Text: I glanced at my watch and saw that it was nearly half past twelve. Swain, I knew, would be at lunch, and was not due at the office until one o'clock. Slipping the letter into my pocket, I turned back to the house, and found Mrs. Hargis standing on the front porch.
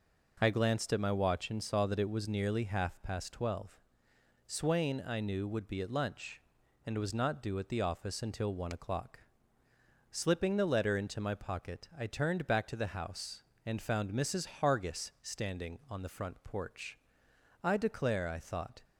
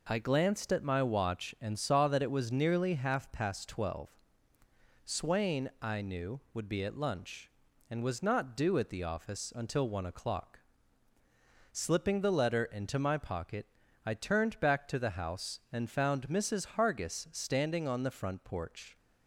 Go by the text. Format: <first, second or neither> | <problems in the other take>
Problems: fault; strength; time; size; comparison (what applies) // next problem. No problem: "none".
second | goes on to say "I declare I thought"; noticeable; from 17.6 s on; 1.2 s long